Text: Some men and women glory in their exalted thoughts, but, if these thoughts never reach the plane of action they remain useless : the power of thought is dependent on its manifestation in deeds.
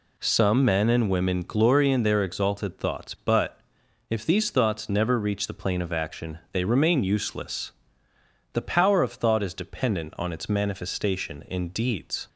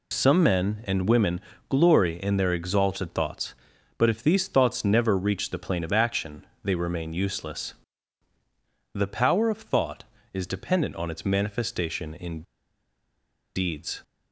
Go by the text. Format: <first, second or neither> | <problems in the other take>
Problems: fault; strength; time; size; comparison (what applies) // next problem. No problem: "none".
first | pauses between "women" and "glory"; slight; at 1.4 s; 0.30 s long // pauses between "action" and "they"; slight; at 6.4 s; 0.18 s long // pauses between "in" and "deeds"; at 12.4 s; 1.1 s long